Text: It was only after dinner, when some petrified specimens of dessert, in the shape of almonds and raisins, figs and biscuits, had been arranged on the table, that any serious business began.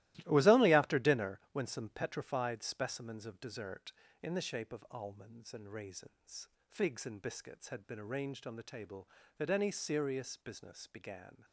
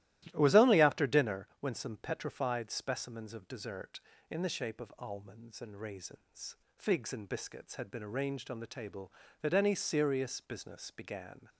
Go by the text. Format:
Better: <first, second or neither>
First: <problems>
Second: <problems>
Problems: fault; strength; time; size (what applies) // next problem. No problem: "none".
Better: second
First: gets quieter; strong; throughout; 10.5 dB // starts louder than the rest; strong; until 1.1 s; 17 dB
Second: starts louder than the rest; strong; until 1.2 s; 15 dB